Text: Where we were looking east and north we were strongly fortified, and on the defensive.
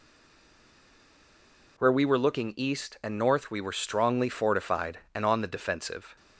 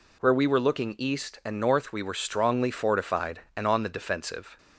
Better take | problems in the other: second | stays silent before the first word; noticeable; until 1.7 s; 1.7 s long

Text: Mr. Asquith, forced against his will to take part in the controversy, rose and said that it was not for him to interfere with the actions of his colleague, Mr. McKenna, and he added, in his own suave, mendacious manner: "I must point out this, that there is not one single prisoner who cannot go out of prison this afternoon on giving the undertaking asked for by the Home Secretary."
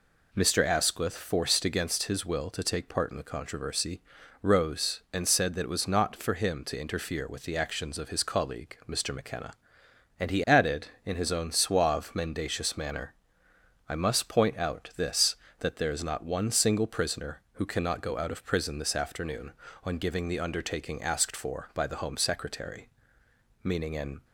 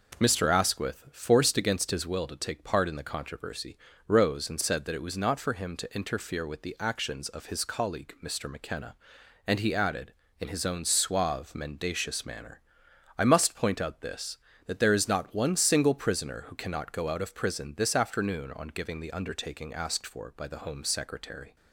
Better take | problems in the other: second | goes on to say "Meaning an"; noticeable; from 23.6 s on; 0.62 s long

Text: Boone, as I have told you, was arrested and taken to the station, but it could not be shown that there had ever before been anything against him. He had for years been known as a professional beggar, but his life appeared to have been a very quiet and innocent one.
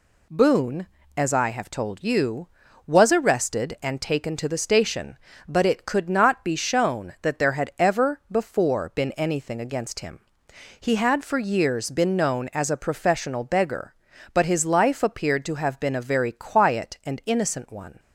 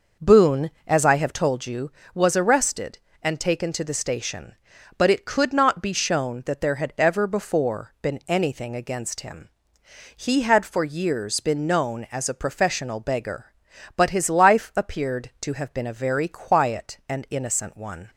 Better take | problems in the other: first | starts louder than the rest; noticeable; until 1.5 s; 5.5 dB

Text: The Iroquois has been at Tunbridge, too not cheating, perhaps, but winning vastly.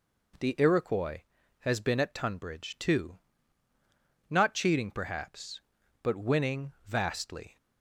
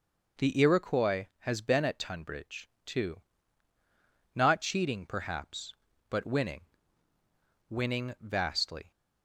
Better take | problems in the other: first | pauses between "too" and "not"; at 3.2 s; 1.1 s long; also in the first // says "winning" twice; at 7.6 s

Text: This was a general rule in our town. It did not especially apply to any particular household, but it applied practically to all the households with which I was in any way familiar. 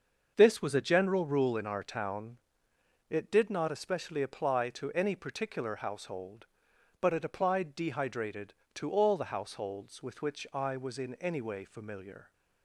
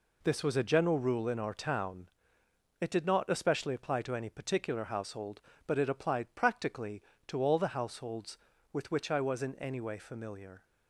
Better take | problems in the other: second | starts louder than the rest; until 1.3 s; 6.5 dB // says "dehydrated" for "practically"; at 7.7 s

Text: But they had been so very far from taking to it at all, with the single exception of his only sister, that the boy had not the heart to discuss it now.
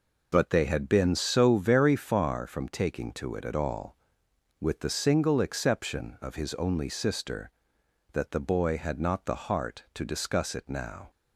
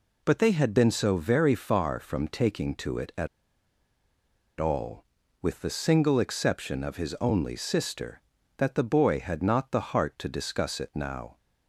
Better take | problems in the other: first | pauses between "at" and "all"; strong; at 3.2 s; 1.3 s long

